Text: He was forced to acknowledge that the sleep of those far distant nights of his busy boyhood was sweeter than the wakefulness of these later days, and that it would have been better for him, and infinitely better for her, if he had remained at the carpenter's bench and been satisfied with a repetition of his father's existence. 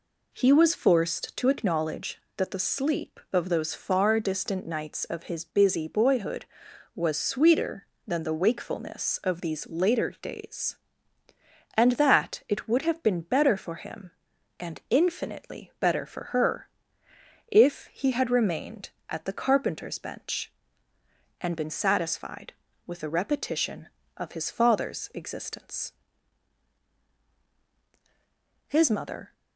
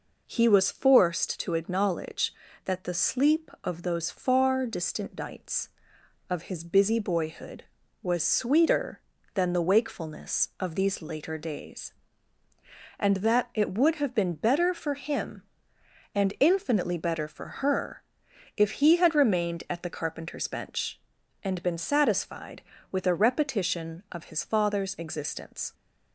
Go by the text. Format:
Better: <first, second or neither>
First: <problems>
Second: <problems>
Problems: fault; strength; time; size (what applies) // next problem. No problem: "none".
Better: second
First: goes on to say "His mother"; noticeable; from 28.6 s on; 0.66 s long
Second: none